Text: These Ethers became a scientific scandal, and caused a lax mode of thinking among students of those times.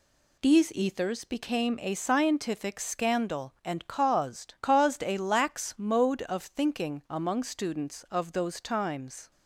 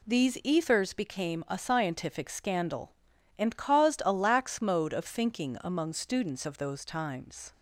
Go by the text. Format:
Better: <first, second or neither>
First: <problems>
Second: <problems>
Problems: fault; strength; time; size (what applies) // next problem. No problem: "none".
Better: second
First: says "caused" twice; at 4.6 s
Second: none